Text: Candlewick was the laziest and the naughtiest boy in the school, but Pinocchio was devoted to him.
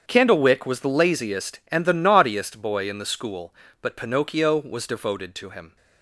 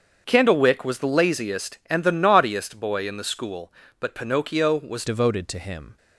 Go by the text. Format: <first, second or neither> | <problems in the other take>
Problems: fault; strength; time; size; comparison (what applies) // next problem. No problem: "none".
first | starts louder than the rest; strong; until 1.2 s; 7 dB; strong in the first // changes voice at "devoted"; from 5.0 s on; 0.9 s long